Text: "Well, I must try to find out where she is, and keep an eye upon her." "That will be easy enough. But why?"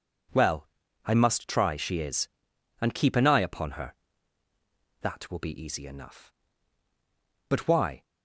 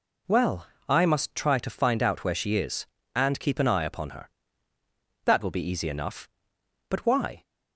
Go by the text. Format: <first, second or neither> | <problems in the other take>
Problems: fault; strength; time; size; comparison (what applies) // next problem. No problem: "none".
second | skips "to find out where"; at 1.7 s